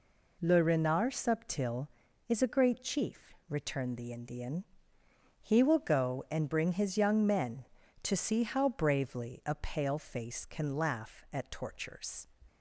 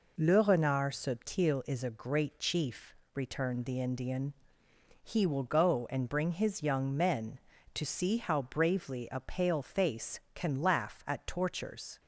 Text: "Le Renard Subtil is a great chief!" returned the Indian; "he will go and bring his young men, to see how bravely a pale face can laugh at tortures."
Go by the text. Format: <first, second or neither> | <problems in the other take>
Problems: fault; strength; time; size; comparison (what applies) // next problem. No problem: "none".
neither | none